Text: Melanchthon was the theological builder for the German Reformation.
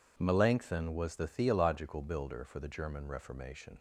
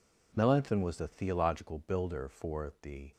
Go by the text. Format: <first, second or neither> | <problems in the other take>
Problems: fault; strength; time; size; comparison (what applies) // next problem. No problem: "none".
first | stops before "German Reformation"; at 3.1 s